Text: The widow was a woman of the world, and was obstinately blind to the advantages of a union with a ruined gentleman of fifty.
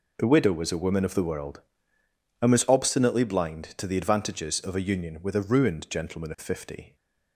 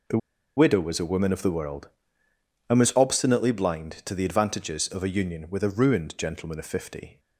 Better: first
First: none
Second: pauses between "The" and "widow"; at 0.1 s; 0.38 s long

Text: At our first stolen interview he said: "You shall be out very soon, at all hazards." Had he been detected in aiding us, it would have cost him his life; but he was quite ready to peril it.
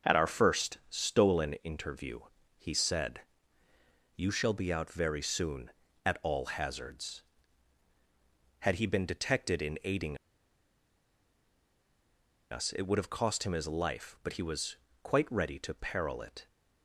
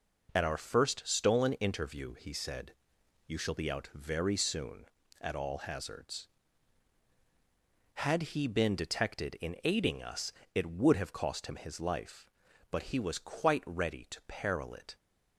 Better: second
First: starts louder than the rest; until 1.2 s; 6.5 dB // pauses between "interview" and "he"; at 2.2 s; 0.38 s long // pauses between "aiding" and "us"; strong; at 10.1 s; 2.3 s long // pauses between "was" and "quite"; slight; at 14.7 s; 0.26 s long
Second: none

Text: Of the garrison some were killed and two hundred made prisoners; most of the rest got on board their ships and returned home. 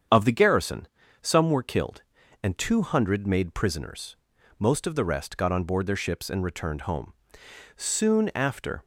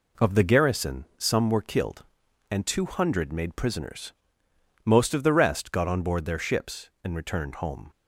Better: second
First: starts louder than the rest; strong; until 1.4 s; 8 dB // pauses between "garrison" and "some"; slight; at 0.8 s; 0.34 s long // goes on to say "Soon after"; noticeable; from 7.7 s on; 1.0 s long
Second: none

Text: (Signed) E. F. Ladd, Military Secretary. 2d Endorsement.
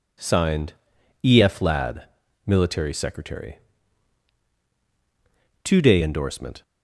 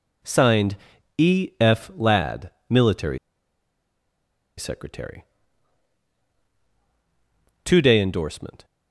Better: first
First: none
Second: pauses between "Military" and "Secretary"; strong; at 3.1 s; 1.4 s long

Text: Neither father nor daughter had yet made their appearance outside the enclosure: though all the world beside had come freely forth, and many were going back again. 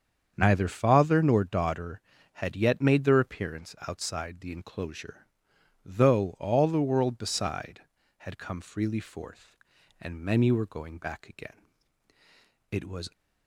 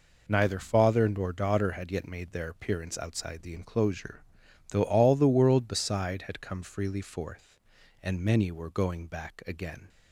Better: second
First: starts louder than the rest; strong; until 1.3 s; 7.5 dB // goes on to say "It was"; slight; from 12.7 s on; 0.40 s long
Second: none

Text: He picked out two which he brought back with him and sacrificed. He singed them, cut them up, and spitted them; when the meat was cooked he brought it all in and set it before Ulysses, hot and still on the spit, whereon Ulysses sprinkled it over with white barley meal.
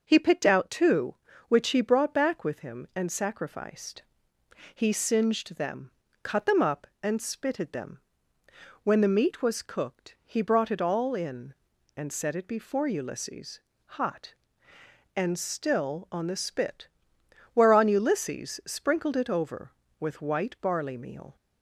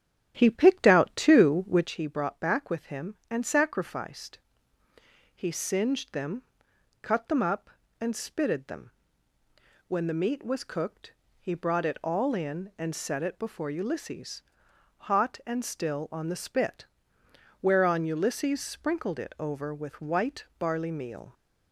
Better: first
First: none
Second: starts louder than the rest; strong; until 1.9 s; 11 dB // pauses between "cooked" and "he"; slight; at 11.1 s; 0.26 s long // pauses between "white" and "barley"; slight; at 20.4 s; 0.16 s long

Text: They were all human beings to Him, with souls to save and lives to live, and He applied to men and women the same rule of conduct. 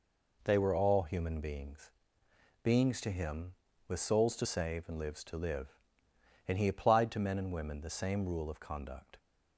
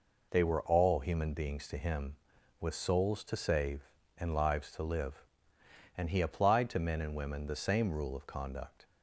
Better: second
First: says "beings" twice; at 2.6 s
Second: none

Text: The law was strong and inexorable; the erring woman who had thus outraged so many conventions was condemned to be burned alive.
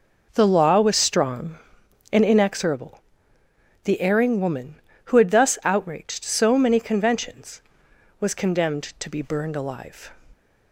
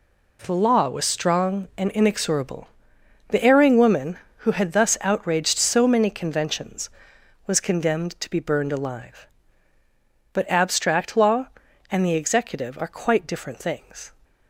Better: first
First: none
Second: goes on to say "But abstract law and the executive are quite different things"; strong; from 10.3 s on; 3.8 s long

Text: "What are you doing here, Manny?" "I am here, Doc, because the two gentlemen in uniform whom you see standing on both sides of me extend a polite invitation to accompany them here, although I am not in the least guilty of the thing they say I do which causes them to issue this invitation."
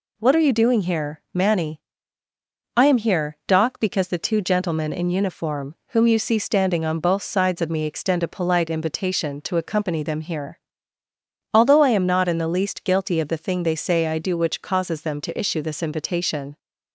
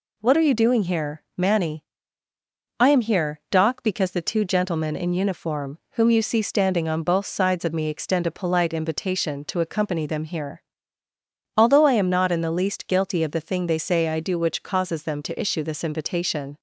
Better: neither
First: none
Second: none

